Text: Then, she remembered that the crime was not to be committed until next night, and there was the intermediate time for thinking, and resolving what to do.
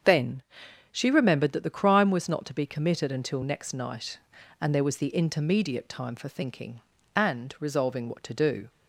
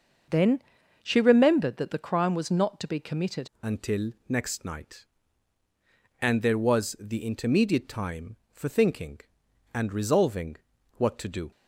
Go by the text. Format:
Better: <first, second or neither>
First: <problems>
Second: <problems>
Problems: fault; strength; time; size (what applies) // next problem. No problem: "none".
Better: first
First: starts louder than the rest; strong; until 1.5 s; 7.5 dB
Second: starts louder than the rest; until 1.7 s; 6 dB // changes voice at "until"; from 3.6 s on; 7.9 s long // pauses between "until" and "next"; slight; at 4.1 s; 0.16 s long // pauses between "resolving" and "what"; at 10.5 s; 0.42 s long